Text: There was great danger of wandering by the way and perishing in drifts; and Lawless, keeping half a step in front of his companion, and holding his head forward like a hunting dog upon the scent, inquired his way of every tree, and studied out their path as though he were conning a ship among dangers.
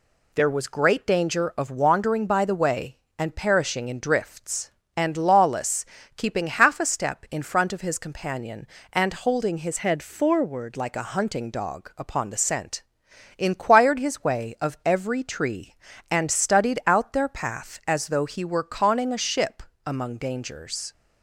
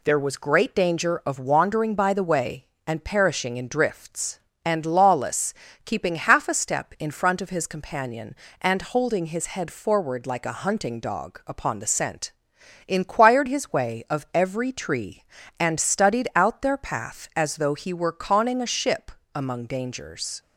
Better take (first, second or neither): second